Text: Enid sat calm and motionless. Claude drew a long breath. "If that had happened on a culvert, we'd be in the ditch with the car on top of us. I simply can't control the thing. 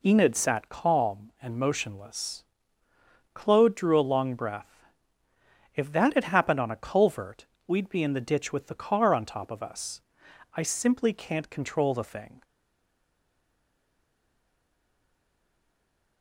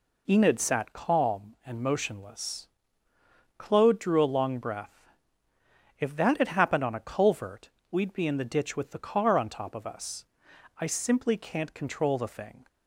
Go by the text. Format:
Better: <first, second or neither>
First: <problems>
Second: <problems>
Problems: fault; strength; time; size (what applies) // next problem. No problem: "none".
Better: second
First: stays silent after the last word; strong; from 12.4 s on; 3.8 s long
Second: none